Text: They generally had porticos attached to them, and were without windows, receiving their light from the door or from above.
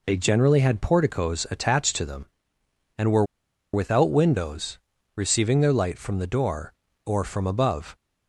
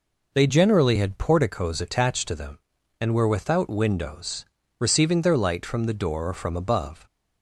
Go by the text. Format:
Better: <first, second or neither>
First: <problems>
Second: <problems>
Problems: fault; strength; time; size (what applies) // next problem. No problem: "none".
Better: second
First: pauses between "were" and "without"; noticeable; at 3.2 s; 0.49 s long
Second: none